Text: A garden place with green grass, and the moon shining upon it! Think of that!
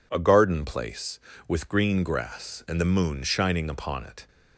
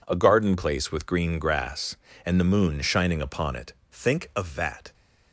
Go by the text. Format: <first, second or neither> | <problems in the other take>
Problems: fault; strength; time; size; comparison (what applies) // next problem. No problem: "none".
second | stops before "Think of that"; at 4.2 s